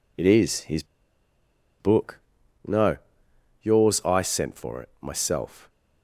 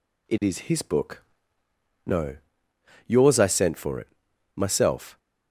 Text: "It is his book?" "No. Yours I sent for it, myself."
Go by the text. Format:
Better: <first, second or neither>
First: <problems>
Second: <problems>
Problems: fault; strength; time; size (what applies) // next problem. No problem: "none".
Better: second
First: pauses between "his" and "book"; noticeable; at 0.8 s; 0.95 s long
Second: none